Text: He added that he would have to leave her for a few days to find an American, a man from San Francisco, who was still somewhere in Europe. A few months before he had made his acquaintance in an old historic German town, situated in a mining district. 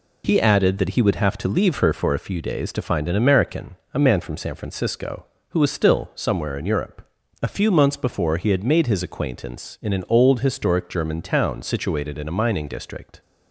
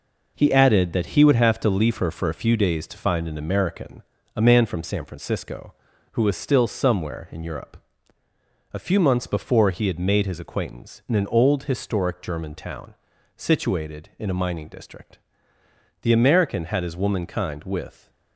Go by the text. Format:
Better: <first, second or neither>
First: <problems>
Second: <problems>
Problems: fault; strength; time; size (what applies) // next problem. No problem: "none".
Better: first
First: none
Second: goes on to say "The American had his womankind with"; strong; from 16.0 s on; 2.0 s long